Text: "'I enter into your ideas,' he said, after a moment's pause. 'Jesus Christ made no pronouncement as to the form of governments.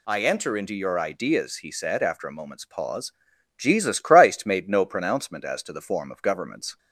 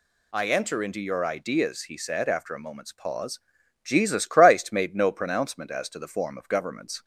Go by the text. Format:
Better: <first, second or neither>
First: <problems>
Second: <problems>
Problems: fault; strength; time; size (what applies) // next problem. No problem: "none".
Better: neither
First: none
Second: none